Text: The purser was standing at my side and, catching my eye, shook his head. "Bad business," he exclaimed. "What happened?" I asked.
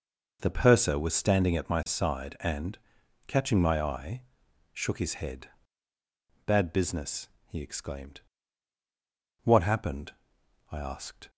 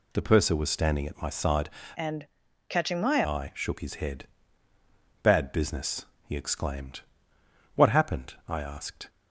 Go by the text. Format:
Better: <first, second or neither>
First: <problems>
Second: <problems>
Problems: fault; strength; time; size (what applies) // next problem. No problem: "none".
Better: first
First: none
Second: changes voice from "and" to "my"; from 1.9 to 3.2 s; 1.3 s long